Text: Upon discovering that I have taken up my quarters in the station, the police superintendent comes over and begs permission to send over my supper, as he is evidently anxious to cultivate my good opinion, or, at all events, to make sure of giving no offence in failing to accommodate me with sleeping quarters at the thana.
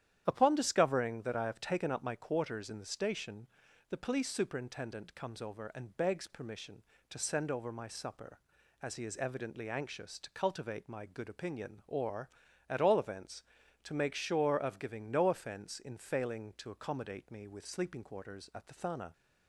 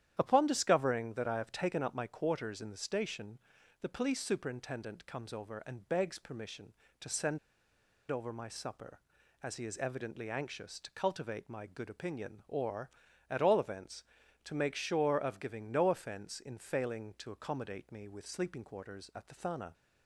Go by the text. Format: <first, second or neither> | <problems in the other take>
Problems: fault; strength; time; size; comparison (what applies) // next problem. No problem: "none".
first | starts louder than the rest; strong; until 1.1 s; 10.5 dB; strong in the first // pauses between "send" and "over"; noticeable; at 7.3 s; 0.70 s long